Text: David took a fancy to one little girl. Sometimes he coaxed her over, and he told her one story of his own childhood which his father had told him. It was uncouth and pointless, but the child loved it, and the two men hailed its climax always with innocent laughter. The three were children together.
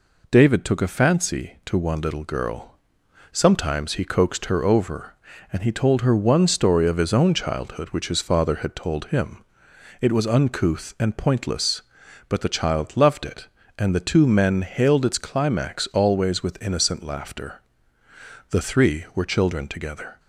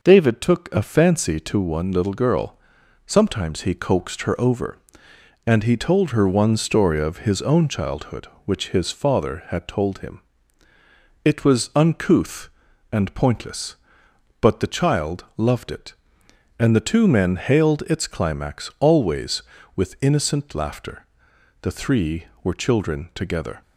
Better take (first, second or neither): neither